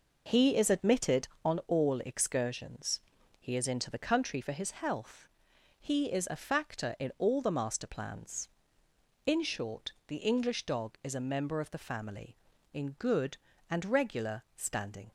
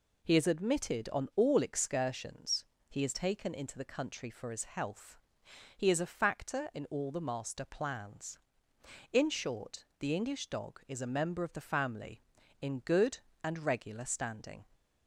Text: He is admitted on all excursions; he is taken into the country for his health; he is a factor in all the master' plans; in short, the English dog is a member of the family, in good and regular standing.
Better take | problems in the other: second | skips "taken"; at 3.6 s

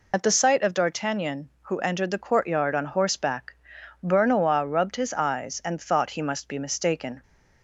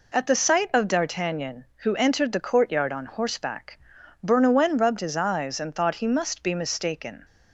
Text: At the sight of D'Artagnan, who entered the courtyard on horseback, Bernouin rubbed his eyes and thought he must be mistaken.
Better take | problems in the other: second | loses the start of "At"; at 0.1 s; 35 ms

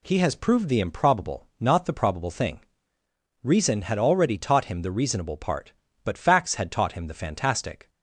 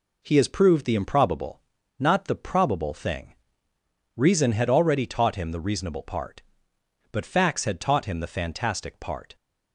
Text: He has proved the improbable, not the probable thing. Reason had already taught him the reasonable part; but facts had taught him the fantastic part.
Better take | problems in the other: second | stops before "part"; at 7.8 s

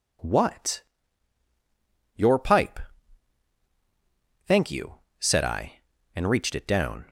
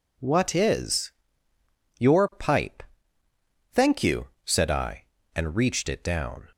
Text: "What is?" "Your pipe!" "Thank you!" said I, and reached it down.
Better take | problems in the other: second | skips "is"; at 1.4 s

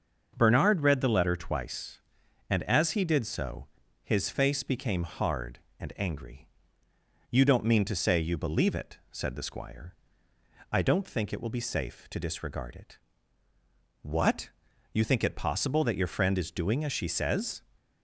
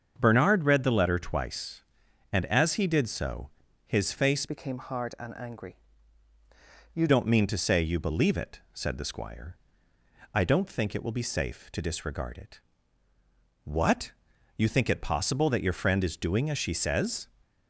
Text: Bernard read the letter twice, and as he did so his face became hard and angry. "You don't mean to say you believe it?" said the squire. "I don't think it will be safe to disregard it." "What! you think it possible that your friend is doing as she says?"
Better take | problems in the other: first | starts louder than the rest; strong; until 1.1 s; 7 dB; also in the first // pauses between "so" and "his"; at 3.4 s; 0.40 s long; also in the first // changes voice from "became" to "You"; from 4.4 to 7.0 s; 2.6 s long

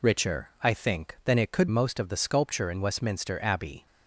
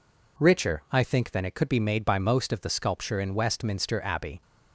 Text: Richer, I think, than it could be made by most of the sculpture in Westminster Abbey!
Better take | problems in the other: second | skips "be made by"; at 1.6 s

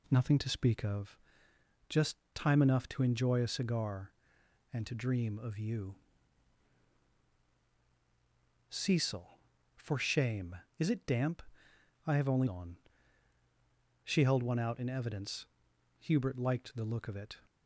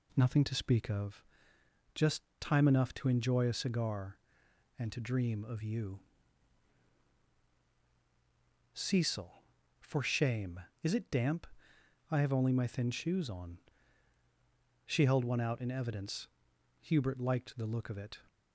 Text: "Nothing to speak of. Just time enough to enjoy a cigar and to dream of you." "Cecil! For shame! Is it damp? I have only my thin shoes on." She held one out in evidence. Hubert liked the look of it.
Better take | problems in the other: second | pauses between "Just" and "time"; slight; at 2.1 s; 0.18 s long; slight in the second // skips "my thin shoes"; at 12.4 s

